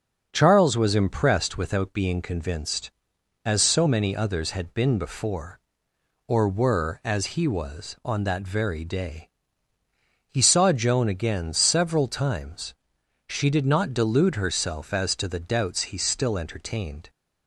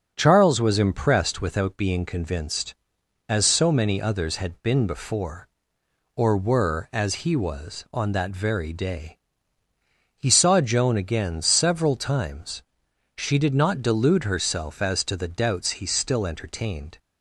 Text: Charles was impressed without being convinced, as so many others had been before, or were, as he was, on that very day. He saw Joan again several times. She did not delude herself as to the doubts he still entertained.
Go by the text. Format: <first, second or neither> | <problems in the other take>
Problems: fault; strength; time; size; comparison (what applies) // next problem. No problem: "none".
neither | starts louder than the rest; the same in both